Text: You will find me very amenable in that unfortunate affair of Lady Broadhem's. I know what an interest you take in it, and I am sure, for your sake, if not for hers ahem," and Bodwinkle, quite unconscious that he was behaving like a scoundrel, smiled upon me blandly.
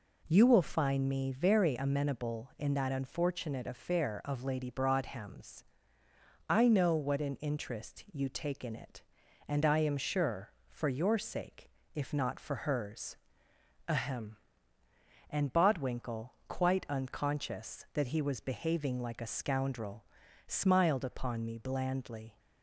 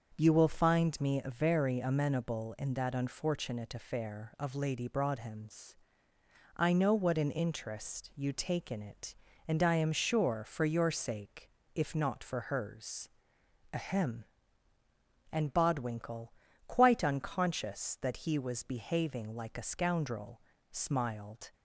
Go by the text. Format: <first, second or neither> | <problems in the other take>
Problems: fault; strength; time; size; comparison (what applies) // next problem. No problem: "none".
first | starts louder than the rest; until 1.1 s; 6.5 dB // pauses between "hers" and "ahem"; noticeable; at 13.0 s; 0.64 s long; noticeable in the first // stops before "upon me blandly"; at 21.5 s